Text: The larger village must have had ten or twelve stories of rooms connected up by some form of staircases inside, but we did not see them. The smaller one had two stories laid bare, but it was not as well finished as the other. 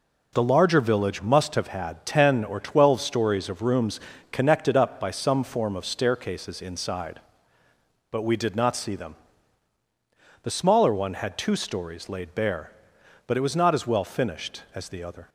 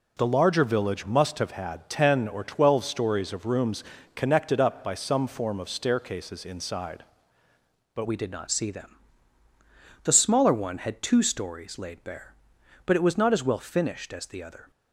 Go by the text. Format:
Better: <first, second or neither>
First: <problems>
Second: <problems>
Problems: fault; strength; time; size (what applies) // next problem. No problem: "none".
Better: first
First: pauses between "rooms" and "connected"; slight; at 3.9 s; 0.32 s long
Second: pauses between "rooms" and "connected"; slight; at 3.8 s; 0.32 s long // changes voice at "we"; from 8.0 s on; 6.7 s long